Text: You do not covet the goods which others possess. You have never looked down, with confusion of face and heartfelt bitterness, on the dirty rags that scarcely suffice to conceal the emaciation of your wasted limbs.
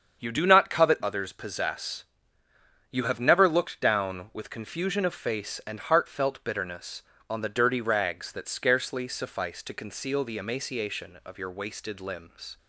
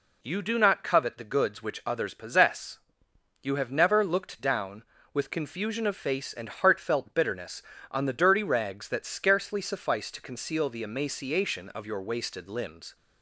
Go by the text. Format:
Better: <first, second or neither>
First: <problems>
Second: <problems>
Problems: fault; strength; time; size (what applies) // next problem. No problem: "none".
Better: second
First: starts louder than the rest; strong; until 1.2 s; 7 dB // skips "the goods which"; at 1.0 s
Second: none